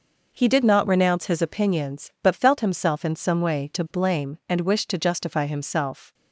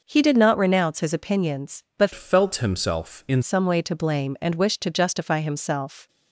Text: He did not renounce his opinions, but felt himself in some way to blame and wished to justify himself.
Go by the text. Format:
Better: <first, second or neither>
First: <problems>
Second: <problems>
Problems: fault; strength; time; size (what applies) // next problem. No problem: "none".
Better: first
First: none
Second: changes voice from "felt" to "in"; from 2.1 to 3.4 s; 1.3 s long